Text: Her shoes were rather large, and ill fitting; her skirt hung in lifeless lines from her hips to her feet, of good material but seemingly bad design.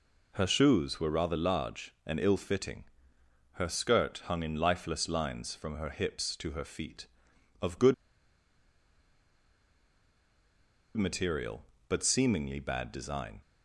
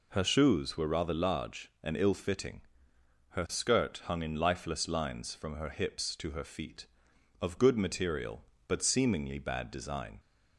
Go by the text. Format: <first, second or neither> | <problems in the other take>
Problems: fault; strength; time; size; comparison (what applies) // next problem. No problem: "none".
second | pauses between "good" and "material"; strong; at 7.9 s; 3.0 s long